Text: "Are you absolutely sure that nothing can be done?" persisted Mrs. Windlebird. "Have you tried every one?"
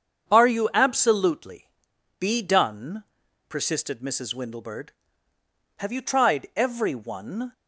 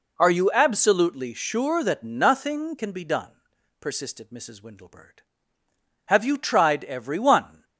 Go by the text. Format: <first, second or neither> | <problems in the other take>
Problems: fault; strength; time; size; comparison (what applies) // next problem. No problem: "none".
second | starts louder than the rest; strong; until 1.3 s; 7 dB // skips "sure that nothing can"; at 1.9 s